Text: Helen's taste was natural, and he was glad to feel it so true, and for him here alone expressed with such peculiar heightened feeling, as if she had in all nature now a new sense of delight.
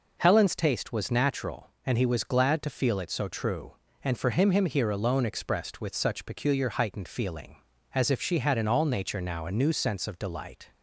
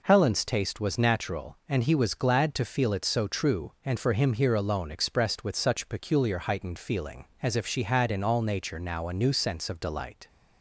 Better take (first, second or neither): second